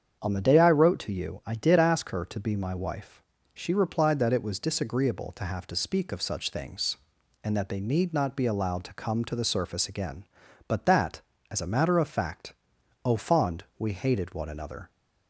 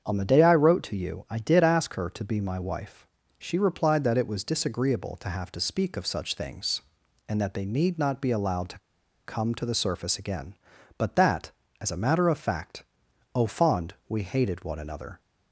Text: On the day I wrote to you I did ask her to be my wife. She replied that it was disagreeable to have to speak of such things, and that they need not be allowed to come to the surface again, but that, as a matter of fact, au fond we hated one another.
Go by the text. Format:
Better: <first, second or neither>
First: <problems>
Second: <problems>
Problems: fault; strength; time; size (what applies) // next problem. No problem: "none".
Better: first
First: starts louder than the rest; strong; until 1.2 s; 7.5 dB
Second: starts louder than the rest; strong; until 1.0 s; 7.5 dB // pauses between "to" and "come"; noticeable; at 8.7 s; 0.47 s long